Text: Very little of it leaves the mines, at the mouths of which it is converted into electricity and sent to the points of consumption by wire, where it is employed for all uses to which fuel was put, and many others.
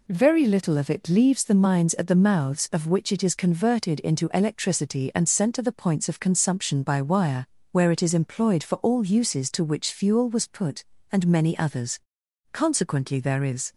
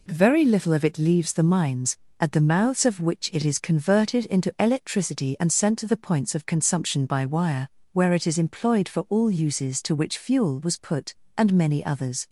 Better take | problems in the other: second | goes on to say "Consequently there is"; noticeable; from 12.5 s on; 1.2 s long

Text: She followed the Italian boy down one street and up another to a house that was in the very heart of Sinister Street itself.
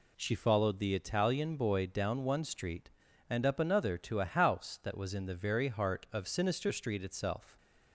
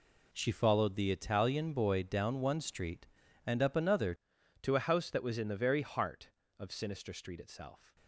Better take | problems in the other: first | changes voice at "to"; from 4.6 s on; 3.3 s long

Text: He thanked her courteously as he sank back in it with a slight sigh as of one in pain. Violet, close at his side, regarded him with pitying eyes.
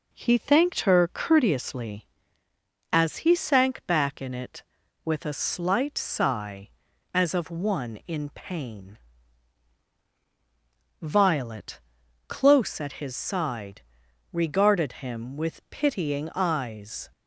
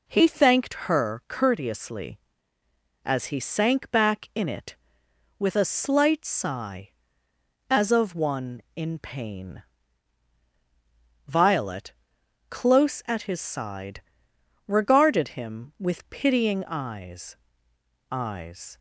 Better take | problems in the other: first | says "eyes" twice; at 18.1 s

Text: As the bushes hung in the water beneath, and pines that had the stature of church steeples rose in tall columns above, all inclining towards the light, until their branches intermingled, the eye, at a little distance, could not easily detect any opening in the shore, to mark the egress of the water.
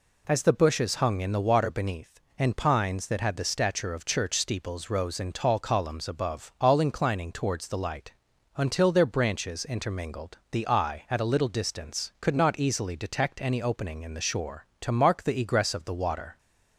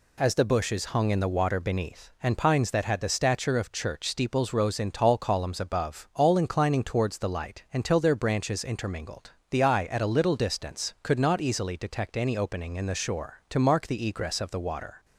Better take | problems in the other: neither | none

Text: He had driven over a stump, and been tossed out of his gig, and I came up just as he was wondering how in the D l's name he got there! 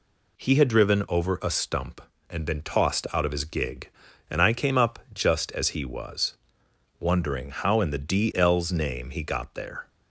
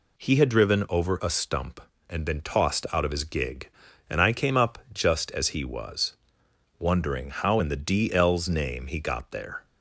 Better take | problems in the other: neither | pauses between "up" and "just"; slight; the same in both // pauses between "was" and "wondering"; noticeable; the same in both

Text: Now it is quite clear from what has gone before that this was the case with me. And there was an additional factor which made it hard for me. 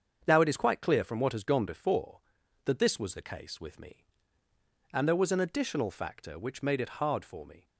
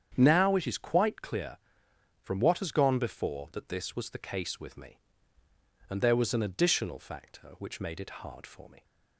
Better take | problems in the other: neither | starts louder than the rest; strong; the same in both

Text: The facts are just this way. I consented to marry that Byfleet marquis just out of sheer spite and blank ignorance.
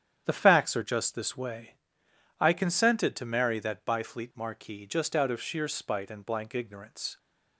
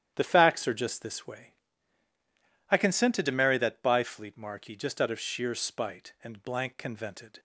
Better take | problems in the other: first | starts louder than the rest; strong; until 1.1 s; 10.5 dB; strong in the first // says "convented" for "ignorance"; at 6.7 s

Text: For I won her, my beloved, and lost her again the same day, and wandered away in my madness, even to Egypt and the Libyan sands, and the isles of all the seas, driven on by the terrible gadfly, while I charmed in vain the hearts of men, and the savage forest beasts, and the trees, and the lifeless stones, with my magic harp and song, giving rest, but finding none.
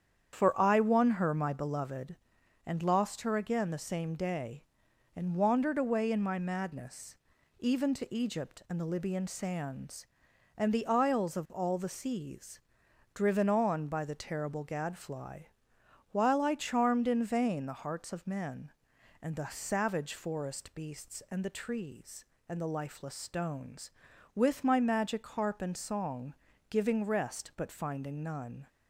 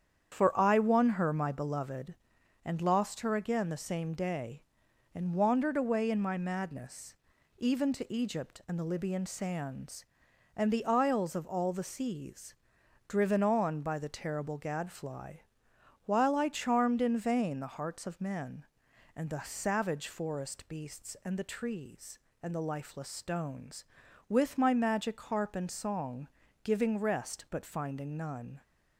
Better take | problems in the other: neither | starts louder than the rest; strong; the same in both

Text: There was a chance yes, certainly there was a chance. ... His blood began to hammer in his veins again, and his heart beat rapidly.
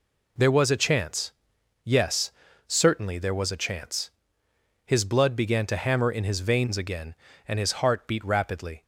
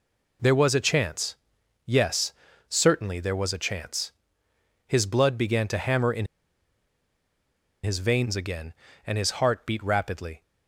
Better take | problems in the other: first | pauses between "chance" and "yes"; noticeable; at 1.3 s; 0.48 s long; noticeable in the first // pauses between "in" and "his"; strong; at 6.2 s; 1.5 s long

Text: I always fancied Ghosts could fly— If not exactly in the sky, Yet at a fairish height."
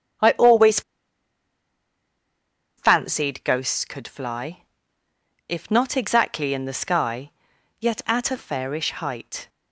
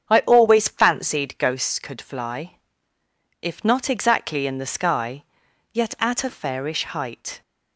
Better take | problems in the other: second | starts louder than the rest; strong; until 3.1 s; 7.5 dB; strong in the second // pauses between "always" and "fancied"; strong; at 0.8 s; 1.9 s long

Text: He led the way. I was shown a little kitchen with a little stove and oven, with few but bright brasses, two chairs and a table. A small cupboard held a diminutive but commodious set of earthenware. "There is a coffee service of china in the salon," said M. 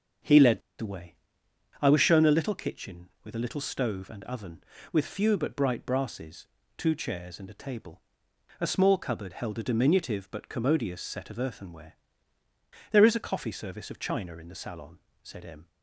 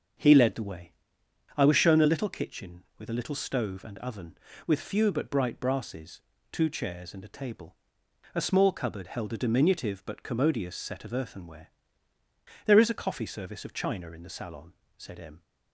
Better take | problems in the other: second | starts louder than the rest; strong; until 2.1 s; 7.5 dB; strong in the second // pauses between "led" and "the"; slight; at 0.6 s; 0.17 s long

